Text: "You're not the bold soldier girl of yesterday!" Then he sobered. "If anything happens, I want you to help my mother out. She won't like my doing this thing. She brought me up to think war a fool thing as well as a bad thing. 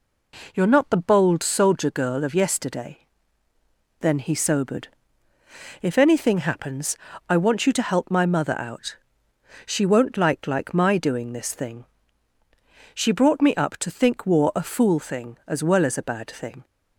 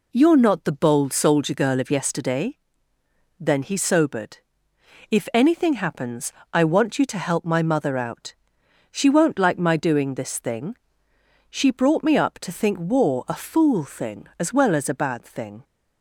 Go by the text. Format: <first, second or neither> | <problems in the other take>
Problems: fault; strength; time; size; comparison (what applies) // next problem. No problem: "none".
second | says "like" twice; at 10.4 s